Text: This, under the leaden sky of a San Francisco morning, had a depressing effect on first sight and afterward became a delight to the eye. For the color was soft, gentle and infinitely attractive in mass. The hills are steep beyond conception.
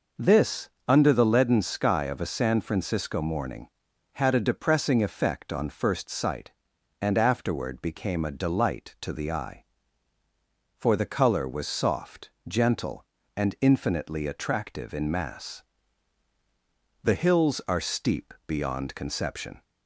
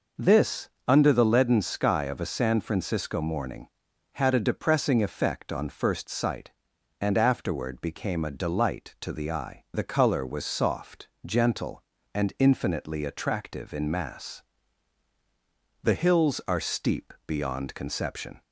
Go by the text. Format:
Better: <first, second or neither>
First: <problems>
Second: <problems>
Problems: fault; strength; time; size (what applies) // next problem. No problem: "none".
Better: first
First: none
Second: skips "For"; at 9.6 s